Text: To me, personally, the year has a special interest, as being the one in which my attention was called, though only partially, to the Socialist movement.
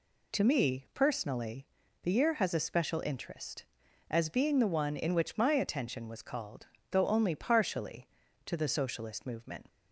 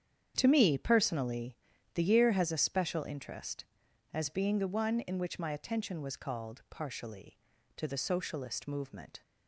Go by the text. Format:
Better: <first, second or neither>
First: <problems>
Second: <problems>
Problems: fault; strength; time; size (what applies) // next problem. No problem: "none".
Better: first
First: none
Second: starts louder than the rest; strong; until 1.3 s; 8.5 dB // skips "though only"; at 6.6 s